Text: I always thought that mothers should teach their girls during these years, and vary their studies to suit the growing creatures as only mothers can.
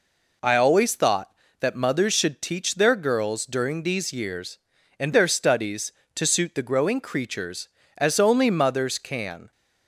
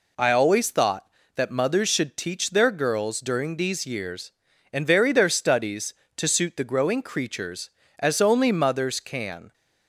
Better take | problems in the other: second | skips "vary"; at 5.1 s

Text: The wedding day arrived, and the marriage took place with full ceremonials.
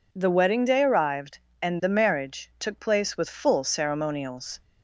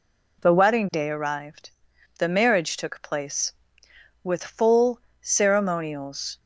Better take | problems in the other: first | skips "and"; at 1.9 s // pauses between "full" and "ceremonials"; slight; at 4.9 s; 0.22 s long

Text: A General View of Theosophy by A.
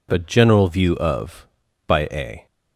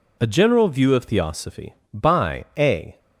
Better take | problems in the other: second | skips "Theosophy"; at 1.6 s

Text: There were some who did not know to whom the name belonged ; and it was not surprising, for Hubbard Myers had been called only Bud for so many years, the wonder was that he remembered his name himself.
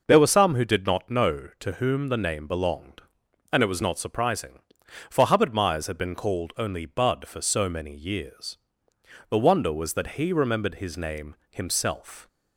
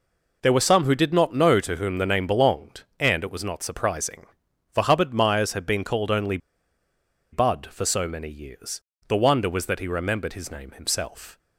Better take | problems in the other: first | pauses between "only" and "Bud"; noticeable; at 6.3 s; 0.94 s long

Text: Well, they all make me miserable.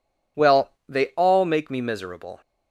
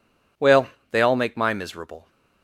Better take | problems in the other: first | says "my" for "me"; at 1.3 s

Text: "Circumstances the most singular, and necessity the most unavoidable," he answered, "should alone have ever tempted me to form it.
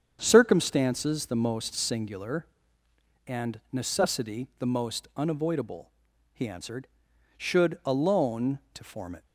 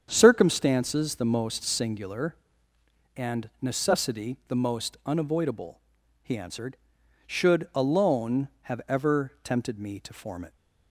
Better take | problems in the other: second | starts louder than the rest; strong; until 1.2 s; 7.5 dB; strong in the second // skips "have ever tempted me"; at 8.6 s

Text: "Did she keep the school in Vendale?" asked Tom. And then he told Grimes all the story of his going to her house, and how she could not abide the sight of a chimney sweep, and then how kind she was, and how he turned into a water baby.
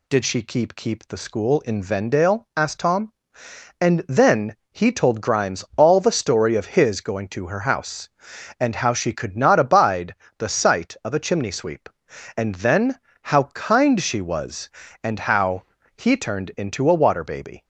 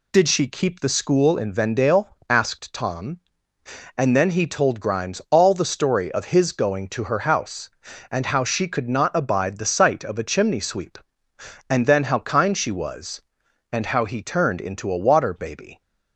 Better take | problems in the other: second | says "keep" twice; at 0.7 s // pauses between "then" and "he"; slight; at 4.5 s; 0.16 s long // pauses between "abide" and "the"; slight; at 10.1 s; 0.24 s long // pauses between "then" and "how"; slight; at 13.0 s; 0.22 s long // pauses between "how" and "he"; slight; at 15.6 s; 0.32 s long

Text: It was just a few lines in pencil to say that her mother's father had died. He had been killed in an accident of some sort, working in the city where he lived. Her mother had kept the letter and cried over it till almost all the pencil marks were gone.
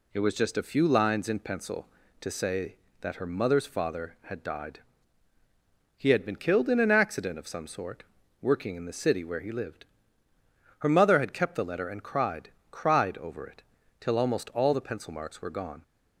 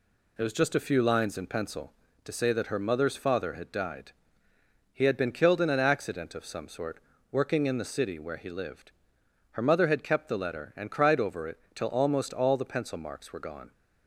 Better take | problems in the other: second | says "cried" twice; at 12.7 s // pauses between "it" and "till"; slight; at 13.6 s; 0.36 s long; slight in the second

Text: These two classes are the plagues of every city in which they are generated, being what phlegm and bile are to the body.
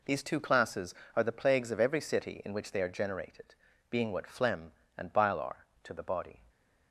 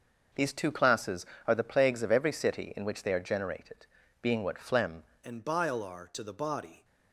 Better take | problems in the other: first | starts louder than the rest; until 1.5 s; 6 dB // changes voice at "and"; from 5.2 s on; 1.6 s long

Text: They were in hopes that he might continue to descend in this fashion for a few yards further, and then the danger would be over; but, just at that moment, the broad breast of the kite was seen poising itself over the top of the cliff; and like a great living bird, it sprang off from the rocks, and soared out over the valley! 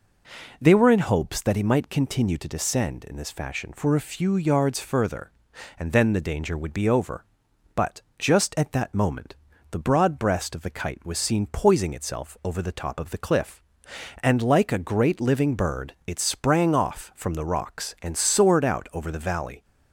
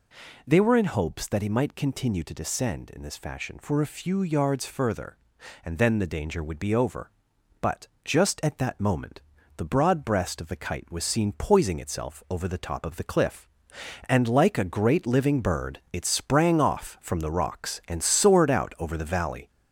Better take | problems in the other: first | gets louder; throughout; 3.5 dB

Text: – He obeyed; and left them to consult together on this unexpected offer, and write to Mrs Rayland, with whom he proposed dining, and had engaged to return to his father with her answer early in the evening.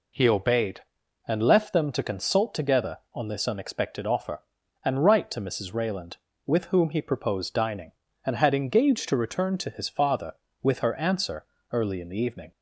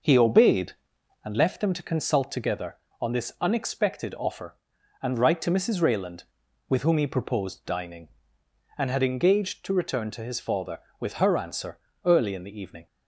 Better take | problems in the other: first | starts louder than the rest; noticeable; until 1.4 s; 6 dB // pauses between "answer" and "early"; slight; at 11.7 s; 0.26 s long; slight in the first

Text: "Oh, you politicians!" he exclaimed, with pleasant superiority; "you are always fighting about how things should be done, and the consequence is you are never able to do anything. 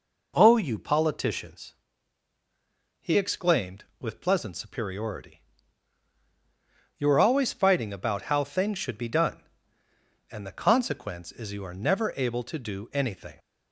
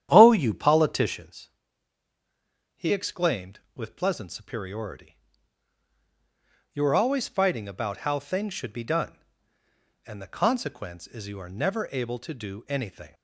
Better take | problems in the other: first | starts louder than the rest; strong; until 1.2 s; 10 dB

